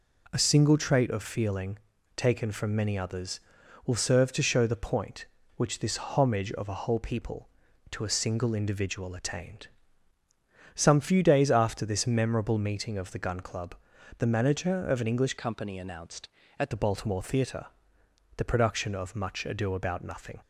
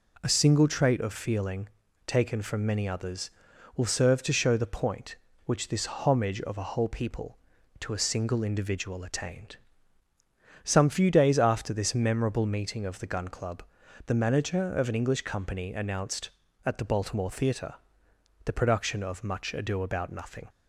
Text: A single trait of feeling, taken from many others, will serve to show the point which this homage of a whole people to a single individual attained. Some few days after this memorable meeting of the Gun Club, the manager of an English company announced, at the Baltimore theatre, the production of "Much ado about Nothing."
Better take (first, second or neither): second